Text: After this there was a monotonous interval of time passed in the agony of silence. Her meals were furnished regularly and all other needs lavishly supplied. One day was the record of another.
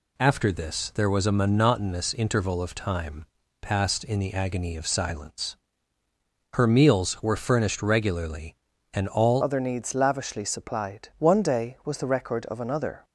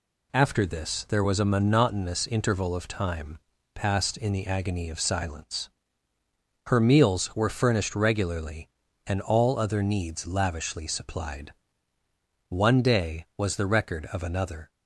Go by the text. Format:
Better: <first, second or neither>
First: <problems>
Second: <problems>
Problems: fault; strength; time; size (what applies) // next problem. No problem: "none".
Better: second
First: pauses between "time" and "passed"; slight; at 3.2 s; 0.34 s long // changes voice at "other"; from 9.4 s on; 3.6 s long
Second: pauses between "time" and "passed"; slight; at 3.3 s; 0.34 s long